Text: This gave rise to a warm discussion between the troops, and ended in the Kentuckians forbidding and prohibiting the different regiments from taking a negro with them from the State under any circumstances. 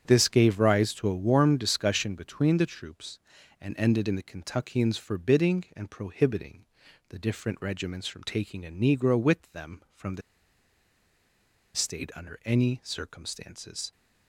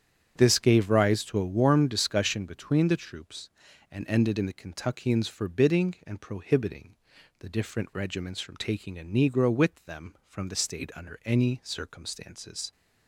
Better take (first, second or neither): second